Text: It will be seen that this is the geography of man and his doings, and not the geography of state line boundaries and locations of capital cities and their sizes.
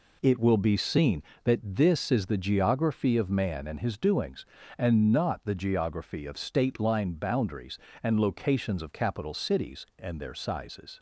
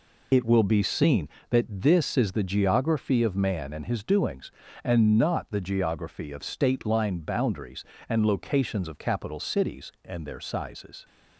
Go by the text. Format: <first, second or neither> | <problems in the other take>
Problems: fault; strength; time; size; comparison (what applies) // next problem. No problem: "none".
first | loses the start of "It"; at 0.3 s; 50 ms